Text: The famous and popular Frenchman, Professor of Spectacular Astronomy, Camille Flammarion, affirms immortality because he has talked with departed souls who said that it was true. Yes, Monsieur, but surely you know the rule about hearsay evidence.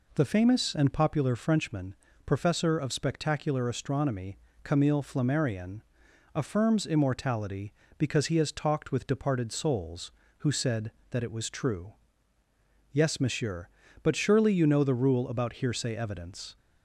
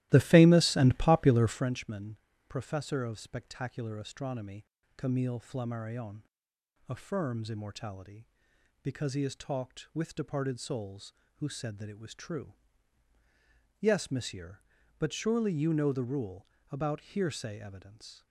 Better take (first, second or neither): first